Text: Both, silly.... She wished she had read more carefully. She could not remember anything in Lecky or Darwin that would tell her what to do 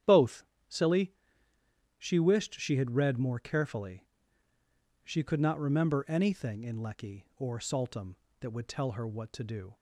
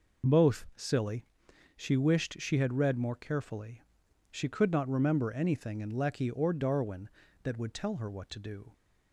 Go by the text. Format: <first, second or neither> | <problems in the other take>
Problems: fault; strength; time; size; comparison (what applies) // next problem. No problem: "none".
second | starts louder than the rest; strong; until 2.1 s; 9.5 dB // says "Saltum" for "Darwin"; at 7.5 s